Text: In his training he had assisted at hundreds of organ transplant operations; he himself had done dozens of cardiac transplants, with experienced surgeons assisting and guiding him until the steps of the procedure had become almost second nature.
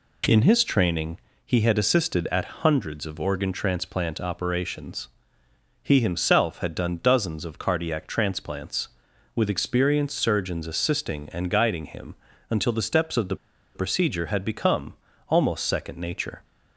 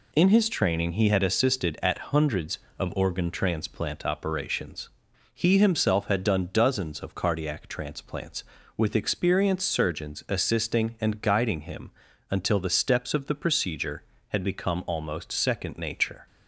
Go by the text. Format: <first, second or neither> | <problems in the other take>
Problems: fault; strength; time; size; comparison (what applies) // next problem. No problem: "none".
second | pauses between "training" and "he"; slight; at 1.1 s; 0.26 s long // pauses between "him" and "until"; slight; at 12.1 s; 0.34 s long; also in the second // pauses between "the" and "procedure"; at 13.3 s; 0.38 s long // pauses between "become" and "almost"; slight; at 14.9 s; 0.36 s long